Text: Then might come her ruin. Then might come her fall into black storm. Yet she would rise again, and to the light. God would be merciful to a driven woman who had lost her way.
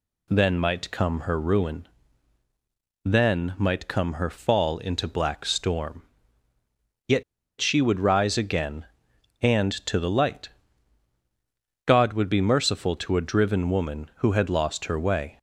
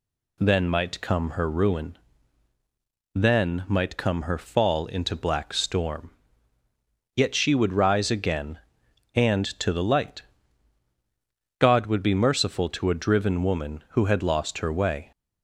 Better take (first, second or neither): second